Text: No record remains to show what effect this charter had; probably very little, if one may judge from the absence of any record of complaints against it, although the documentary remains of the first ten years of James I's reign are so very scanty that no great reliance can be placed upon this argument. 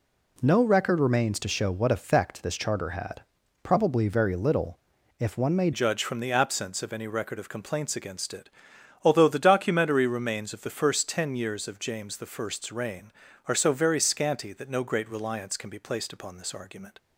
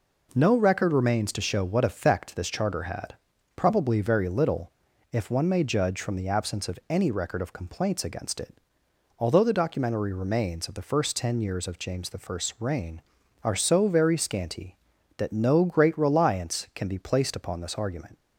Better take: second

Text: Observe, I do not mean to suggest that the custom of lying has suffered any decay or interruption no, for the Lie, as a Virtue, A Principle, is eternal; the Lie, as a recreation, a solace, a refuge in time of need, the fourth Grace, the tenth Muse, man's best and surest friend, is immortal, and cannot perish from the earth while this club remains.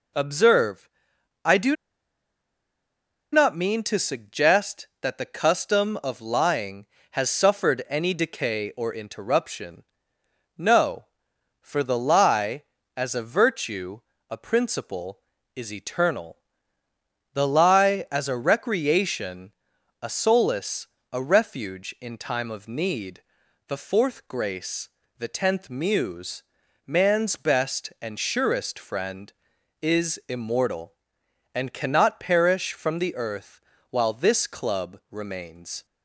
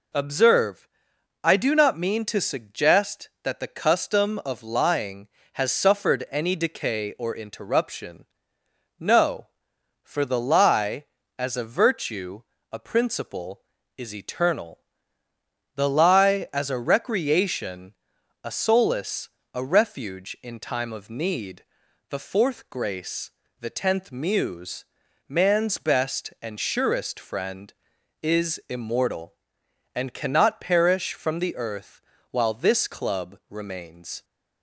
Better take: second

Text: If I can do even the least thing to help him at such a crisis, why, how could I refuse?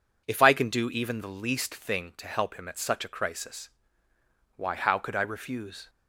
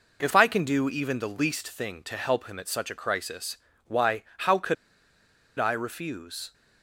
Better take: first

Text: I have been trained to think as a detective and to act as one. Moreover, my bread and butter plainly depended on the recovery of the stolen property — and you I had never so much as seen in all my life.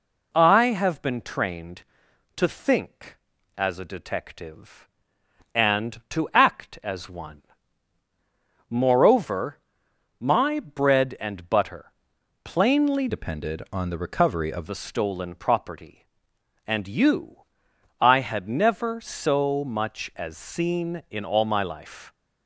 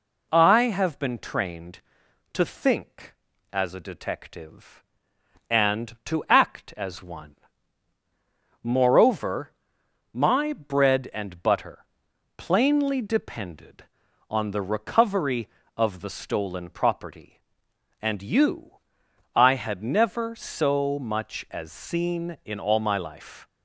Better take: second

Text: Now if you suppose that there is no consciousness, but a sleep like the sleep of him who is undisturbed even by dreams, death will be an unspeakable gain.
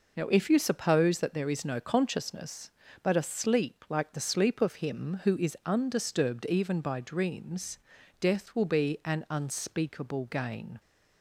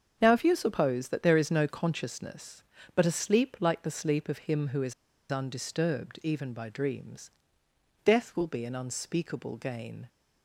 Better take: first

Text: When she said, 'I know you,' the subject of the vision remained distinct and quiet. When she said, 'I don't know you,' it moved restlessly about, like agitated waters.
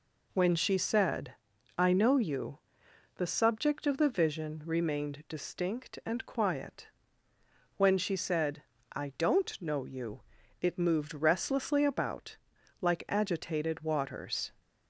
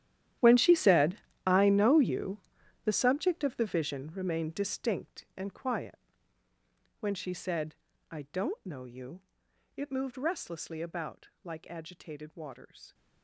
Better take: first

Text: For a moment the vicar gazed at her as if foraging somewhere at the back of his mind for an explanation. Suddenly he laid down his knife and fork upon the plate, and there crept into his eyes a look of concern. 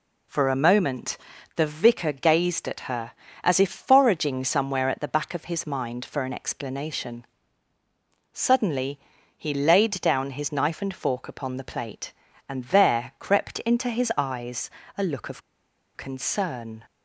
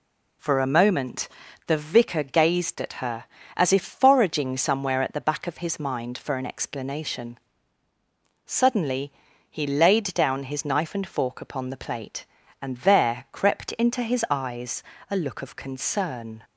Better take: second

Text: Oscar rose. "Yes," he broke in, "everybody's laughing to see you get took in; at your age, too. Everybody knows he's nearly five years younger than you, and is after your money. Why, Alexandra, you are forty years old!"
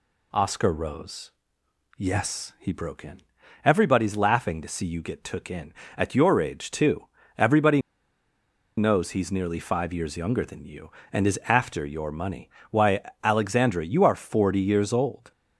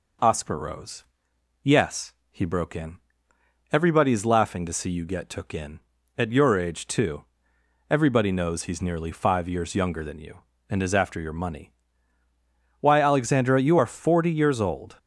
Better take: second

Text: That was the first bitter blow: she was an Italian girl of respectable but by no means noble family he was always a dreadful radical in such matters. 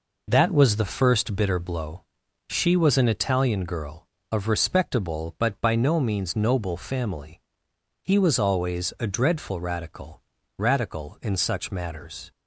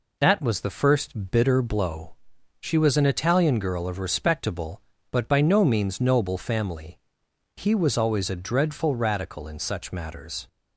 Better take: second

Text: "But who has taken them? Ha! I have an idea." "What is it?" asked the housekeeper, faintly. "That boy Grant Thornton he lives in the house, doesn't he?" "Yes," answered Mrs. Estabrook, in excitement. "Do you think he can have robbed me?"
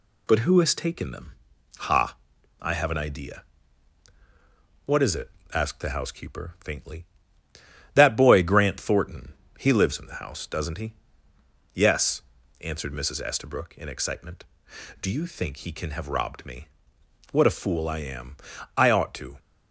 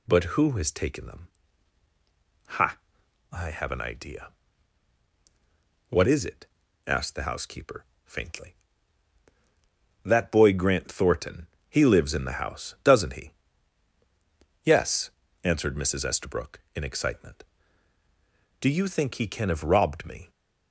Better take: second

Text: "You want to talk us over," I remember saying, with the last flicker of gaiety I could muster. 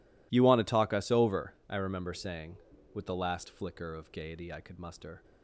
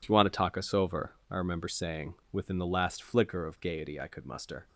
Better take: first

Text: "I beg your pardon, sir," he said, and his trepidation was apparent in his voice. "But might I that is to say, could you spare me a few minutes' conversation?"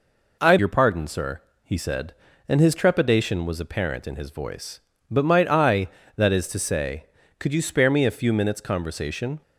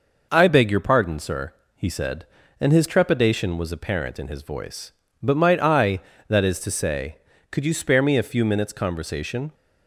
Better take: second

